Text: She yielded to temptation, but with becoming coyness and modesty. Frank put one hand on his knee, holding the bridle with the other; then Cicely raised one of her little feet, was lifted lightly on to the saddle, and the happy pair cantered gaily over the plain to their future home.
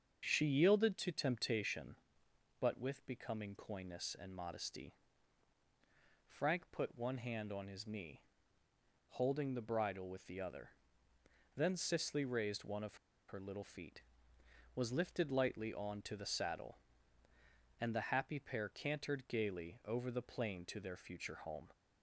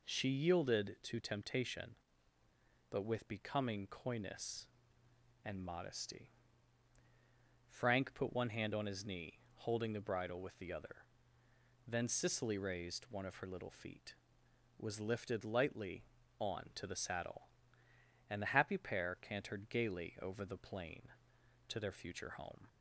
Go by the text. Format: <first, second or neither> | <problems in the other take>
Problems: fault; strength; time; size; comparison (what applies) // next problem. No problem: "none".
second | starts louder than the rest; until 1.2 s; 6.5 dB // pauses between "of" and "her"; slight; at 12.9 s; 0.32 s long